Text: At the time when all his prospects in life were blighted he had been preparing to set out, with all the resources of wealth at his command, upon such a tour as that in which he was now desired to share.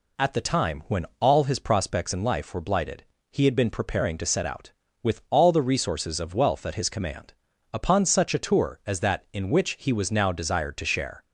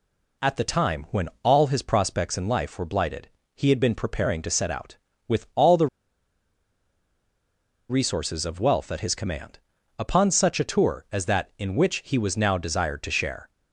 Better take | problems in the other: first | pauses between "blighted" and "he"; slight; at 3.2 s; 0.28 s long; slight in the first // pauses between "the" and "resources"; strong; at 5.8 s; 2.0 s long

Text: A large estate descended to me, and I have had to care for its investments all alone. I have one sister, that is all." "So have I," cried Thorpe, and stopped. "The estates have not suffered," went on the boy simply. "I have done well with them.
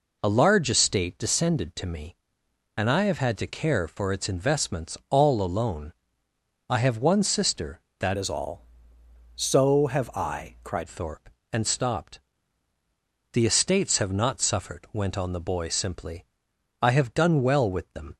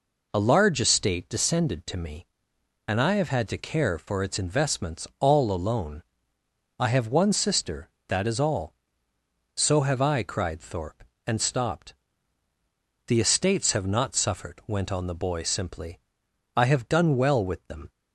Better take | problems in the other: second | changes voice from "is" to "cried"; from 8.1 to 10.8 s; 2.7 s long

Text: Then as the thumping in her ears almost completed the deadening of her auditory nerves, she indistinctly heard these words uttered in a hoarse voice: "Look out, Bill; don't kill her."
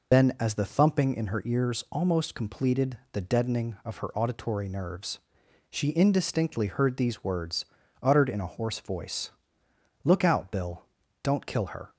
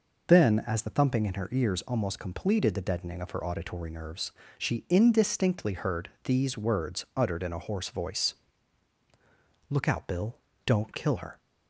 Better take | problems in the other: second | loses the start of "Then"; at 0.1 s; 60 ms // pauses between "completed" and "the"; slight; at 2.9 s; 0.16 s long // pauses between "words" and "uttered"; at 7.6 s; 0.38 s long

